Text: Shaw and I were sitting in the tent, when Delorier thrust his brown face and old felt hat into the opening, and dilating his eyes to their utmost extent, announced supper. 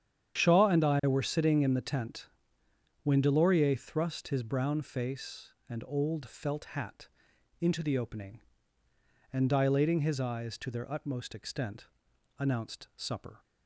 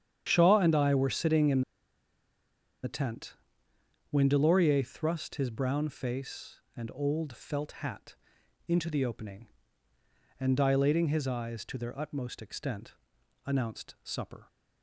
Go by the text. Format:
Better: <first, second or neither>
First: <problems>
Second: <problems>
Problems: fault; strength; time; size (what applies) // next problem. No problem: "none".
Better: first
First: starts louder than the rest; strong; until 1.4 s; 9 dB // pauses between "hat" and "into"; noticeable; at 7.0 s; 0.52 s long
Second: starts louder than the rest; strong; until 1.3 s; 9 dB // pauses between "in" and "the"; at 1.6 s; 1.2 s long // pauses between "hat" and "into"; noticeable; at 8.1 s; 0.52 s long